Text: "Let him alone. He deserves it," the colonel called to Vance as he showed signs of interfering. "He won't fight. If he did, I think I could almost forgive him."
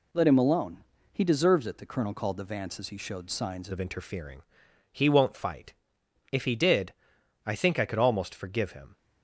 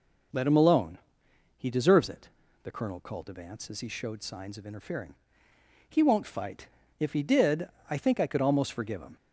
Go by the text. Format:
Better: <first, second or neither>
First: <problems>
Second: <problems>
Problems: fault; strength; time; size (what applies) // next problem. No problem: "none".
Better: second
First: changes voice at "of"; from 3.7 s on; 5.2 s long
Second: none